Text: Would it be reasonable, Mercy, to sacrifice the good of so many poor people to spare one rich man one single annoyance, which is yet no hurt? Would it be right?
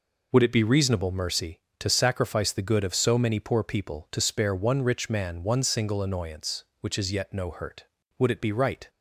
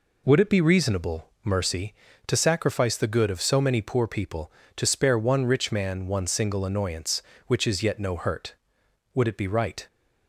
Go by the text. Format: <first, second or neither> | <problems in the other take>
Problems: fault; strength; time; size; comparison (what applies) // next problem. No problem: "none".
neither | none